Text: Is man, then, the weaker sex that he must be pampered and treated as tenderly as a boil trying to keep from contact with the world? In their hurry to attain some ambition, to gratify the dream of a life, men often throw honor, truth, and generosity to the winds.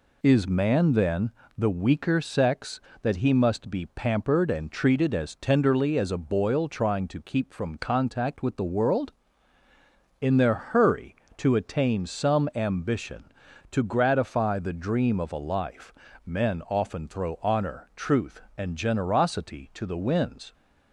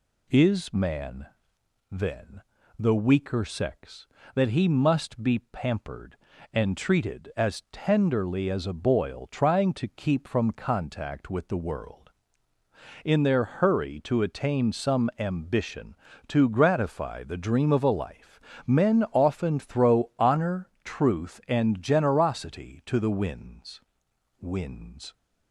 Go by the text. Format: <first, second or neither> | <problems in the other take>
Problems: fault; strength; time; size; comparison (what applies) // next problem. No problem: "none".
first | says "winds" twice; at 24.3 s